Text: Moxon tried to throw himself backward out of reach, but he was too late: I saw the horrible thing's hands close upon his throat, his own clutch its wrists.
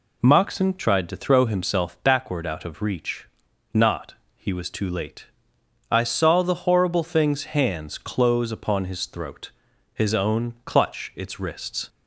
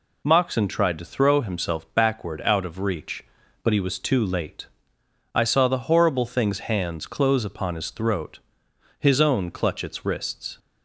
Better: second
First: says "not" for "but"; at 3.7 s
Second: none

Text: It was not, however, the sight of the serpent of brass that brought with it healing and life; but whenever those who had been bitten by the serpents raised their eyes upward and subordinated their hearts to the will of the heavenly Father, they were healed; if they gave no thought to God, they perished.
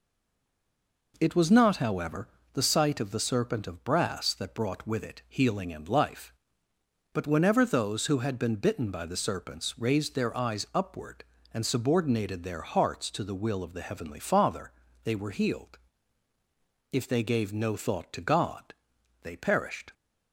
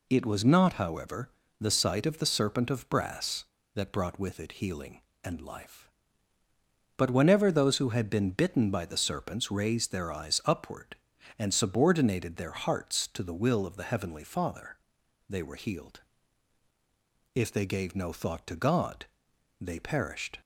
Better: second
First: stays silent before the first word; until 1.1 s; 1.1 s long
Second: none

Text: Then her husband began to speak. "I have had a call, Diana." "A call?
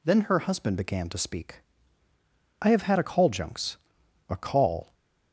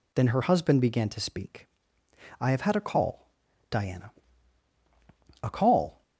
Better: second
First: says "Junks" for "Diana"; at 3.2 s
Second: none

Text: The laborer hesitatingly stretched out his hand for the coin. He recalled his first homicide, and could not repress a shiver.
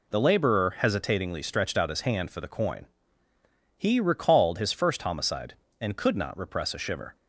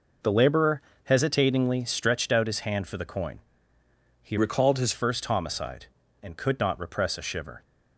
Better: first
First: none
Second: pauses between "laborer" and "hesitatingly"; slight; at 0.8 s; 0.24 s long // changes voice from "recalled" to "his"; from 4.3 to 4.9 s; 0.6 s long

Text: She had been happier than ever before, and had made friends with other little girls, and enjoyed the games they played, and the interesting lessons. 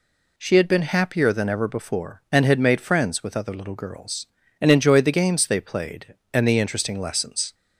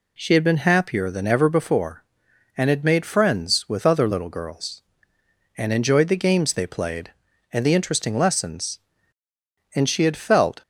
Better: first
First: none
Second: goes on to say "And she had felt"; noticeable; from 9.7 s on; 0.88 s long

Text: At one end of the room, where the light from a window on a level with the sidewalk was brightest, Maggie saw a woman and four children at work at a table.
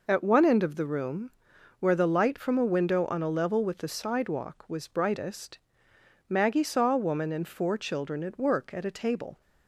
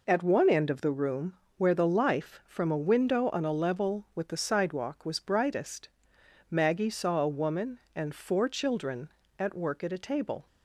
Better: first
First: none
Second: says "life" for "light"; at 1.8 s

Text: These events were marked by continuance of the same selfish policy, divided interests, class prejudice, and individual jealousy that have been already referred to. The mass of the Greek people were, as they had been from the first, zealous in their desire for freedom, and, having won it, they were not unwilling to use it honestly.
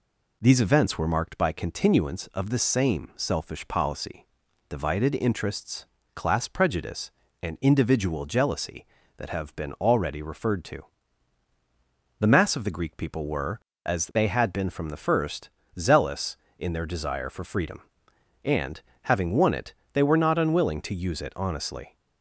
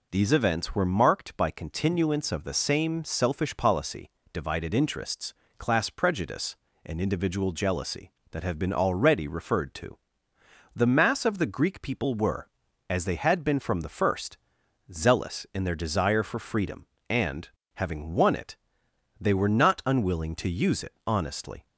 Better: neither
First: none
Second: none

